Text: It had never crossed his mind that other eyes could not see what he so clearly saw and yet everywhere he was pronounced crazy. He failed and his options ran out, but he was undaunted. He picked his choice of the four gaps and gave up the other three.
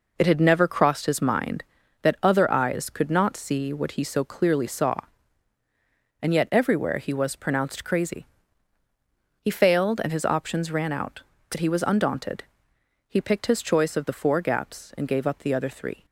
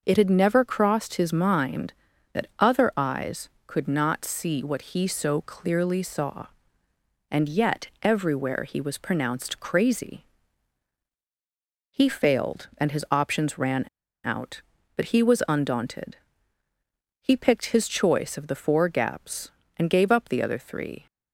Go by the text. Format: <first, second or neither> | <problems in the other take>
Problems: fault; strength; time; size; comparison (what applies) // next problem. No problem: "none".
first | starts louder than the rest; until 1.0 s; 6.5 dB // pauses between "ran" and "out"; at 13.8 s; 0.41 s long